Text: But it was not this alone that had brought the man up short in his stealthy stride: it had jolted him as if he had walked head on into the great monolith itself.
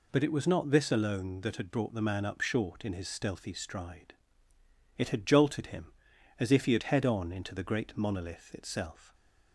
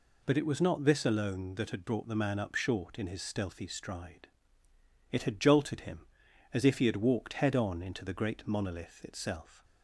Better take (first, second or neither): second